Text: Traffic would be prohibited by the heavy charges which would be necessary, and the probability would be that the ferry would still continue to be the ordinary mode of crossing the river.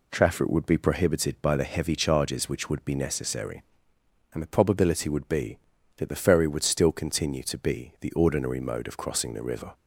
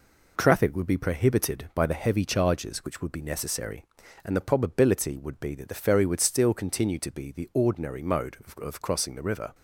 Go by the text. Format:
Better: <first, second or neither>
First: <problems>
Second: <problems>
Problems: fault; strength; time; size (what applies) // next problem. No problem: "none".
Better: first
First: none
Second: says "of" twice; at 8.6 s